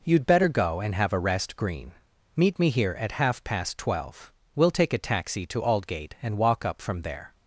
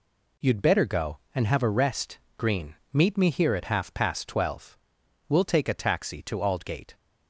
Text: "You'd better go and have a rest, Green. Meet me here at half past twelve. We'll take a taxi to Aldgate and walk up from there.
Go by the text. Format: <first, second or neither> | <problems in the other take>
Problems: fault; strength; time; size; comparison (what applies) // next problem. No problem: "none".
first | stops before "and walk up from there"; at 6.9 s